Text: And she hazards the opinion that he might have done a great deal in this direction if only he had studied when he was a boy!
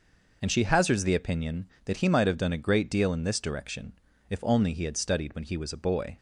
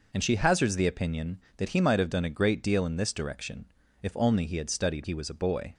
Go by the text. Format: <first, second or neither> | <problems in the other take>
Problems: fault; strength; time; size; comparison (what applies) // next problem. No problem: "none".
first | pauses between "direction" and "if"; slight; at 3.6 s; 0.36 s long; slight in the first // skips "when"; at 5.0 s